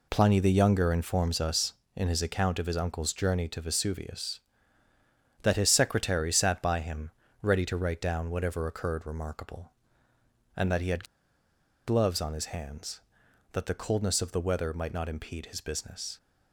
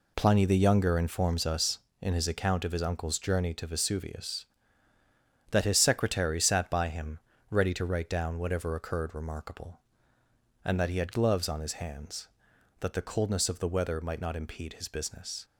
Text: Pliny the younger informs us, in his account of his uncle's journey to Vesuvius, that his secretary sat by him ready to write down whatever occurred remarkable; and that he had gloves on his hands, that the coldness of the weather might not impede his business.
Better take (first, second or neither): second